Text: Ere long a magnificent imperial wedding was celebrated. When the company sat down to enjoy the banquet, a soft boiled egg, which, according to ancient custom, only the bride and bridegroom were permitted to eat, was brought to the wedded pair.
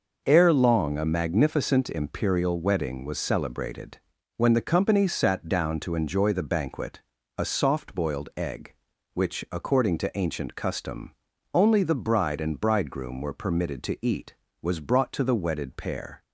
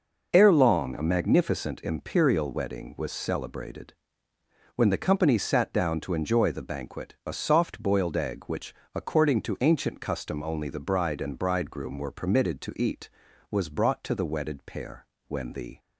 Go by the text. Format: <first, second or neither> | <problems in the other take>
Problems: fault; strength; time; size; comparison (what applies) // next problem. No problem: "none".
first | goes on to say "When the"; from 15.2 s on; 0.50 s long